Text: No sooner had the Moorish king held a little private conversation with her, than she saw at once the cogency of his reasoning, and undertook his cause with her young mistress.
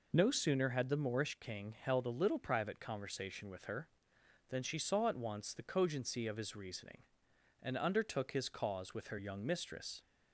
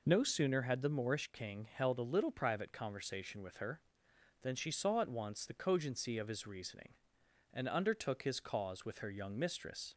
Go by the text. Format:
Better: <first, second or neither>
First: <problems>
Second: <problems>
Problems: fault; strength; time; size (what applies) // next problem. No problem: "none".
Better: neither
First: none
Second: none